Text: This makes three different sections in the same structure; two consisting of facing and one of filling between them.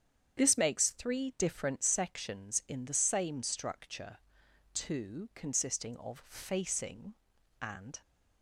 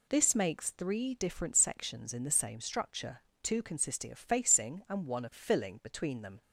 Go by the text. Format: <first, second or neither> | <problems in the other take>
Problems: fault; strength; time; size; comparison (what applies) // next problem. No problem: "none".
second | starts louder than the rest; strong; until 1.4 s; 8 dB // stops before "one of filling between them"; at 8.0 s